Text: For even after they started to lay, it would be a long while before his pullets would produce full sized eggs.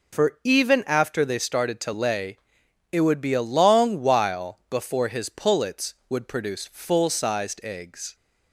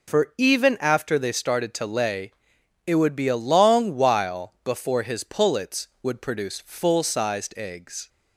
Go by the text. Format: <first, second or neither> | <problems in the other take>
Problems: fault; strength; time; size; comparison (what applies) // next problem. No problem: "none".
neither | none